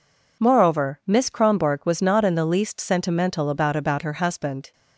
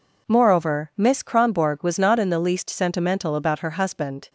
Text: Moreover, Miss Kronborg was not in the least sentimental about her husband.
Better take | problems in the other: second | says "about" twice; at 3.7 s

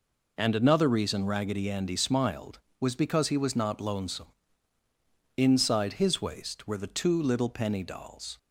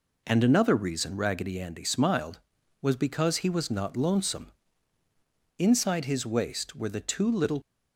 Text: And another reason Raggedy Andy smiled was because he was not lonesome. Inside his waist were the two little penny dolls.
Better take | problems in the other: first | stops before "penny dolls"; at 7.6 s

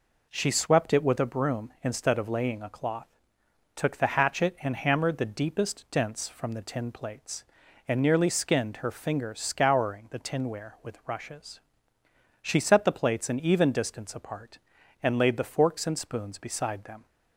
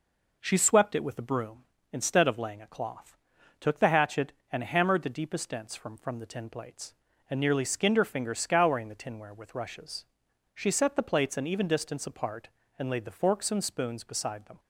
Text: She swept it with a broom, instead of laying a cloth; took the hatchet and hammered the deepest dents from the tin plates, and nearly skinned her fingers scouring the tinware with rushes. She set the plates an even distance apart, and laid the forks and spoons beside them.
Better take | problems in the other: first | says "from" twice; at 5.9 s

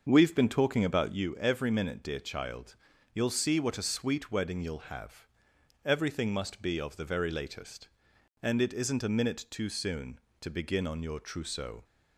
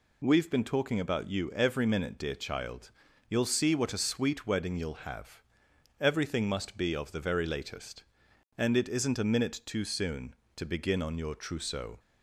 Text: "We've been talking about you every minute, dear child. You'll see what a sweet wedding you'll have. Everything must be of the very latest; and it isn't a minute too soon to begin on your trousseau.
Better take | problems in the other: second | starts louder than the rest; until 1.3 s; 6 dB

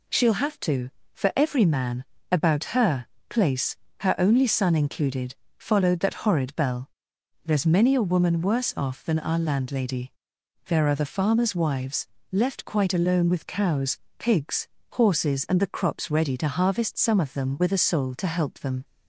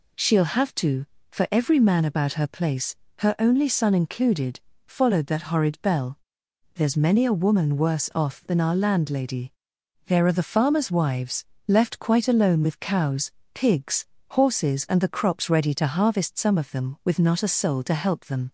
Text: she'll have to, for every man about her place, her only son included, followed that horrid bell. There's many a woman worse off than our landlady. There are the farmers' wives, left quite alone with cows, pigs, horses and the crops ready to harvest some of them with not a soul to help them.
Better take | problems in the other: second | pauses between "man" and "about"; slight; at 2.0 s; 0.26 s long // pauses between "her" and "place"; slight; at 3.0 s; 0.22 s long // skips "not"; at 17.7 s

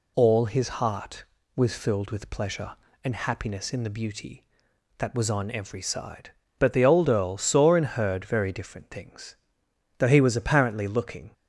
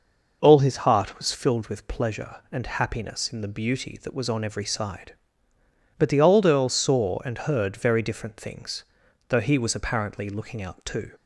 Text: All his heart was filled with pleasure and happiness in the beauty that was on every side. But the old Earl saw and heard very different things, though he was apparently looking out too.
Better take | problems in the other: second | stops before "out too"; at 11.3 s

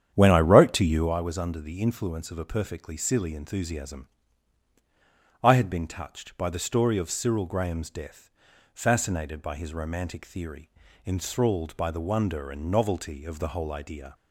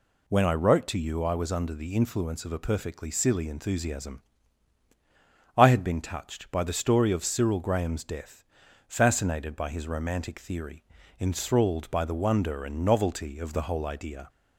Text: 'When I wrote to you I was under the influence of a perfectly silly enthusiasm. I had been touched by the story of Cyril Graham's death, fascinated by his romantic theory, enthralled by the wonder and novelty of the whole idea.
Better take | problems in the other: second | starts louder than the rest; strong; until 1.2 s; 9 dB

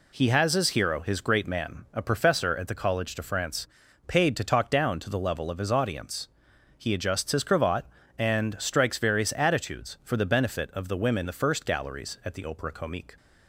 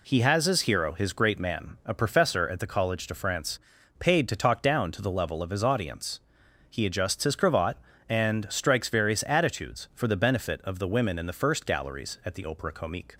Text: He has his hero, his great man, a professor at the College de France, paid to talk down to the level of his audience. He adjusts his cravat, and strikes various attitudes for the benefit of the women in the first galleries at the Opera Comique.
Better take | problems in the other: second | skips "in"; at 11.2 s

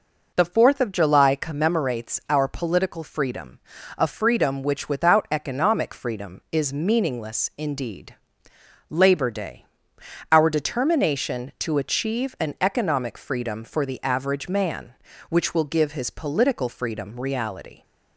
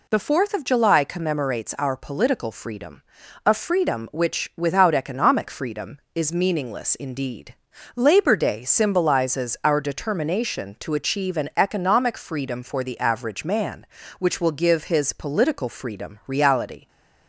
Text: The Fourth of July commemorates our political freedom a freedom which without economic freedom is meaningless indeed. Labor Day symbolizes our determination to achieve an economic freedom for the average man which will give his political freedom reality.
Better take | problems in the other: second | pauses between "freedom" and "a"; at 3.5 s; 0.40 s long; also in the second // skips "symbolizes"; at 9.9 s

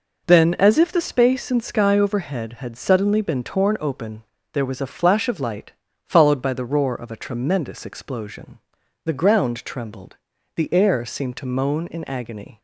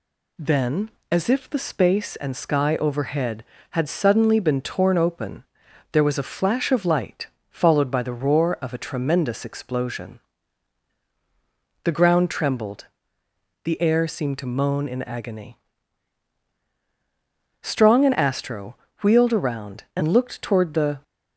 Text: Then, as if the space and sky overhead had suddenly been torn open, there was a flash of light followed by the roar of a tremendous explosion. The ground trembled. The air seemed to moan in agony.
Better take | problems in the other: first | pauses between "light" and "followed"; slight; at 7.2 s; 0.24 s long; slight in the first // goes on to say "Strong and Astro wheeled around and looked toward the"; strong; from 17.6 s on; 3.4 s long

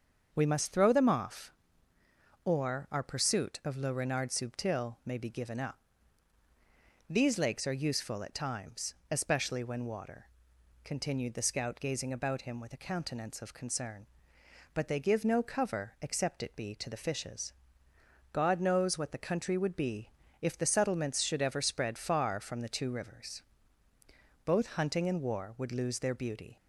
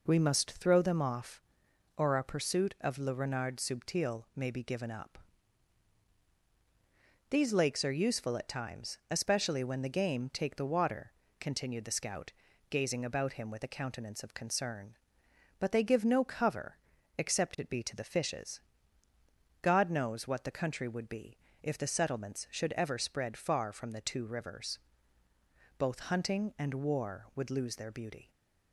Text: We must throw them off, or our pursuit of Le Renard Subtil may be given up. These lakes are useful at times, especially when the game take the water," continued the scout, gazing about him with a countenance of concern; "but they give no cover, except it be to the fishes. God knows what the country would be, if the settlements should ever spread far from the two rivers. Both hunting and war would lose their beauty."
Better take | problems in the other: second | starts louder than the rest; until 1.3 s; 6.5 dB // skips "the game take the"; at 9.8 s

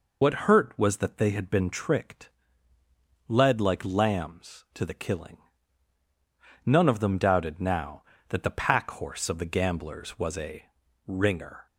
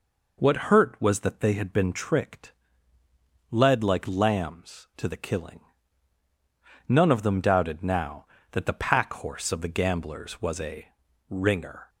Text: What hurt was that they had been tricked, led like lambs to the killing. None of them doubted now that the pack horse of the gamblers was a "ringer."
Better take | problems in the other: second | loses the start of "What"; at 0.2 s; 50 ms // pauses between "a" and "ringer"; at 10.6 s; 0.42 s long; also in the second

